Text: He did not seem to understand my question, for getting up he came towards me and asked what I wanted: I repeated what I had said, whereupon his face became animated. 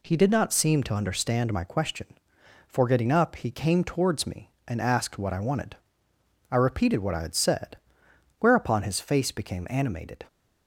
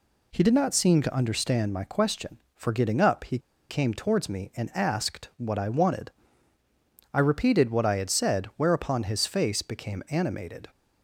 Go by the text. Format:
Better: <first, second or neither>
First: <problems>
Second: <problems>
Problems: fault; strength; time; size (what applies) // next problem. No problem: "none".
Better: first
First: none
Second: pauses between "he" and "came"; slight; at 3.3 s; 0.30 s long